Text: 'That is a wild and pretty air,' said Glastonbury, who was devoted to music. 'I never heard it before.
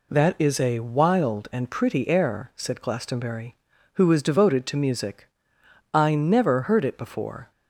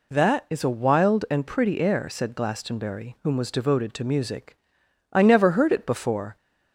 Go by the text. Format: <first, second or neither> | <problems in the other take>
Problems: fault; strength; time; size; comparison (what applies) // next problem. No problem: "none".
first | says "whom" for "who"; at 3.2 s